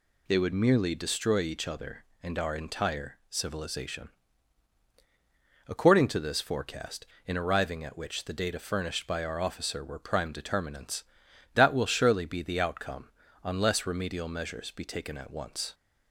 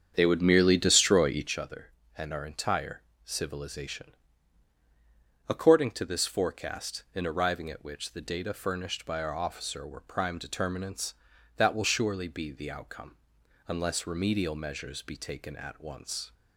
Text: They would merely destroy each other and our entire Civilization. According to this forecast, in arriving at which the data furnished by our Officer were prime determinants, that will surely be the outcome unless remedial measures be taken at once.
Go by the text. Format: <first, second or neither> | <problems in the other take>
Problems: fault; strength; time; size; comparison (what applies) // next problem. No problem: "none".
first | starts louder than the rest; strong; until 1.5 s; 8 dB // pauses between "entire" and "Civilization"; slight; at 3.0 s; 0.26 s long; slight in the first // pauses between "outcome" and "unless"; noticeable; at 13.1 s; 0.50 s long; slight in the first